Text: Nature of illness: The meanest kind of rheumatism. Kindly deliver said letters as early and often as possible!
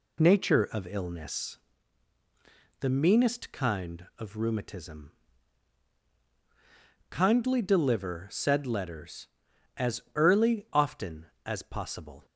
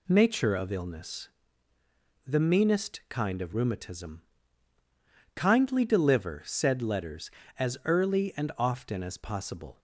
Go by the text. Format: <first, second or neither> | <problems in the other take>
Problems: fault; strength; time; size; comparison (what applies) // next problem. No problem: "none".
second | pauses between "as" and "early"; slight; at 10.0 s; 0.16 s long // skips "and"; at 10.6 s